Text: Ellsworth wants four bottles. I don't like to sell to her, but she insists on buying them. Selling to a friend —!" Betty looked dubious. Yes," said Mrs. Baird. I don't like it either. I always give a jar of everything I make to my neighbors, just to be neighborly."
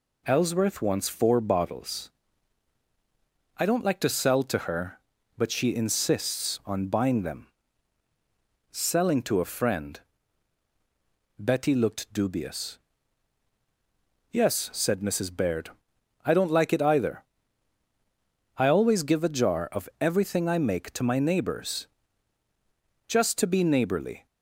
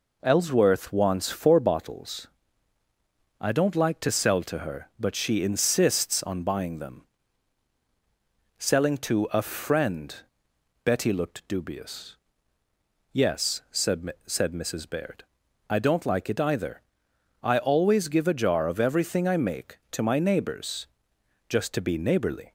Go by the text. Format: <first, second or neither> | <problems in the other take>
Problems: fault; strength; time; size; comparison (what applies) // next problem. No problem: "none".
first | says "said" twice; at 14.2 s